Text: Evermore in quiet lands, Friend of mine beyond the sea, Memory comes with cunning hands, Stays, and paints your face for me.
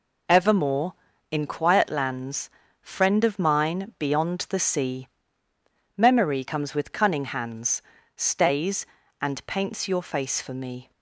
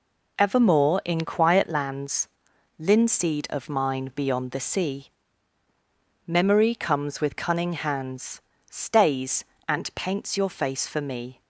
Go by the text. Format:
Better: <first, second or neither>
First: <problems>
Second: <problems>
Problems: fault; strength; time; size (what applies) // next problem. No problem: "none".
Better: first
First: none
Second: says "Linseed" for "Friend"; at 2.7 s